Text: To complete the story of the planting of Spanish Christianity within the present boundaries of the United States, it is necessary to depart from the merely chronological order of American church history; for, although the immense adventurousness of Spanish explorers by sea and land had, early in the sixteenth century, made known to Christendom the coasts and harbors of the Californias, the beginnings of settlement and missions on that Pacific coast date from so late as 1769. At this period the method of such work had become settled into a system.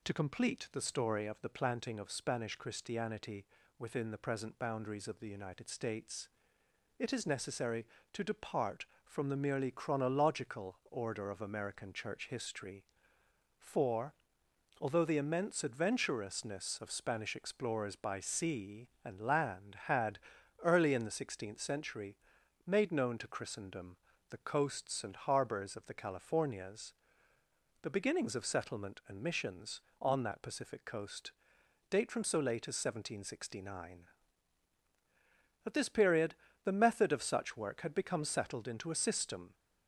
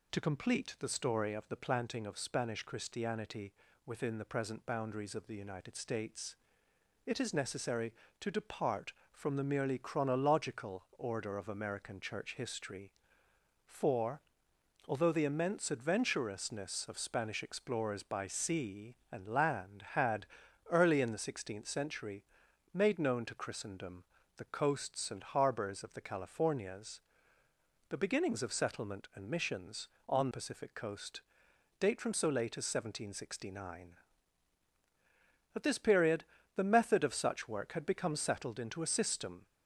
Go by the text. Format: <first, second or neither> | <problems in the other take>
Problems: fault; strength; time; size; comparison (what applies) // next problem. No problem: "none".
first | pauses between "Christianity" and "within"; slight; at 3.5 s; 0.34 s long; slight in the first // pauses between "Christendom" and "the"; slight; at 24.0 s; 0.34 s long; slight in the first // skips "that"; at 30.3 s // pauses between "coast" and "date"; noticeable; at 31.2 s; 0.58 s long; noticeable in the first // pauses between "period" and "the"; slight; at 36.2 s; 0.30 s long; slight in the first